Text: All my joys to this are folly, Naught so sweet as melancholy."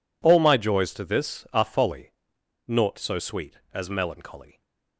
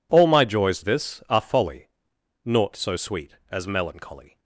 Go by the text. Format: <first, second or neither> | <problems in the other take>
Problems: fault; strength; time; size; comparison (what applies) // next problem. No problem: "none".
first | skips "to"; at 0.8 s